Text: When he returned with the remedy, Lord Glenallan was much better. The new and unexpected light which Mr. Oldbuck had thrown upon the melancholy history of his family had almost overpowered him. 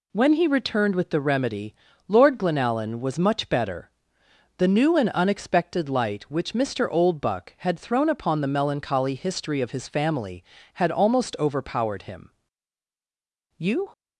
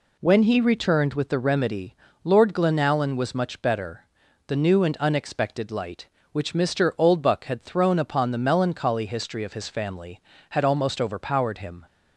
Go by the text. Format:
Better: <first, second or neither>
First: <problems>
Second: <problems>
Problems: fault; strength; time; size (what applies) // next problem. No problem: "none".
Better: second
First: goes on to say "You"; slight; from 13.5 s on; 0.32 s long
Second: none